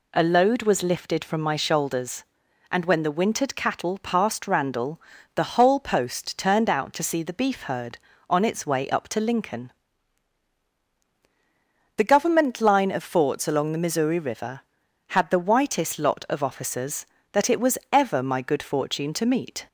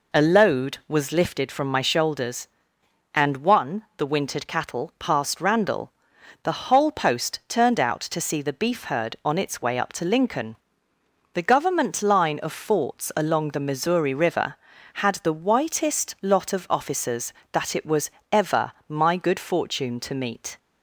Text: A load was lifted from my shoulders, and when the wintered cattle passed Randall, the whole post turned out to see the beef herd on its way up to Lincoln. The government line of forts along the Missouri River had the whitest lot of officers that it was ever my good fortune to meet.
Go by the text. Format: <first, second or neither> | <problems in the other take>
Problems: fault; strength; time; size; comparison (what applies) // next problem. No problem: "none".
first | says "one" for "when"; at 3.3 s // pauses between "was" and "ever"; slight; at 18.0 s; 0.24 s long // pauses between "ever" and "my"; slight; at 18.7 s; 0.18 s long